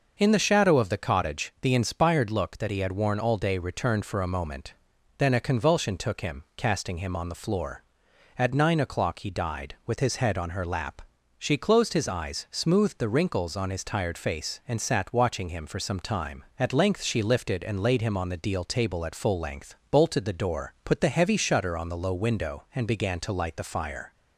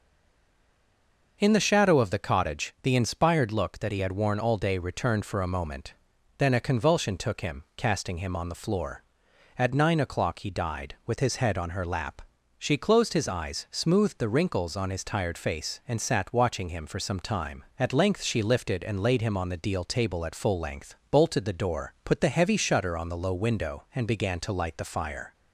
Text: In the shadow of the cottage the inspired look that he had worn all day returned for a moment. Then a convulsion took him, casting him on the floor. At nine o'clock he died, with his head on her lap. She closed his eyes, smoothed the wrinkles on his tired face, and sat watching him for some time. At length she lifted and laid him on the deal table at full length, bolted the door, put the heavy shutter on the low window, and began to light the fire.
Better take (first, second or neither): first